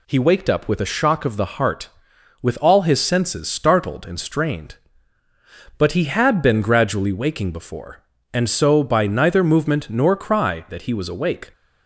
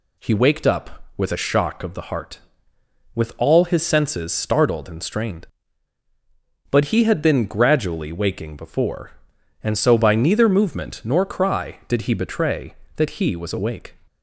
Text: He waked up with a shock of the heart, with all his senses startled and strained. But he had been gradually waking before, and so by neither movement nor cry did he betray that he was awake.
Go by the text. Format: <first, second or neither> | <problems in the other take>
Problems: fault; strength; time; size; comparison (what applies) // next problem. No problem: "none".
second | skips "did he betray"; at 10.6 s